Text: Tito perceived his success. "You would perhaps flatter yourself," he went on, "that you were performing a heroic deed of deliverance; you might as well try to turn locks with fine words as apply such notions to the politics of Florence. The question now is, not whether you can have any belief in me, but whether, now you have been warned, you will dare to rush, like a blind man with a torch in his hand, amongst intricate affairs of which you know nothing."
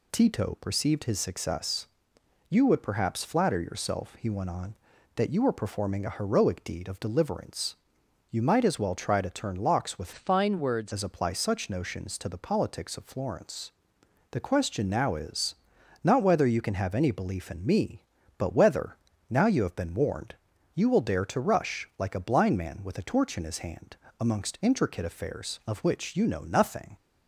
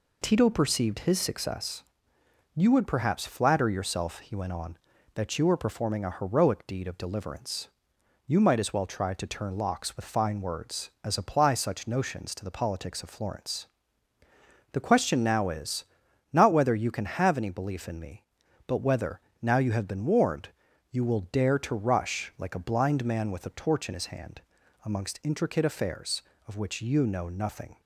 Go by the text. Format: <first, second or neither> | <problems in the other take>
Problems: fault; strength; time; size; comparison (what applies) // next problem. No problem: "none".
second | changes voice from "fine" to "words"; from 10.1 to 10.9 s; 0.8 s long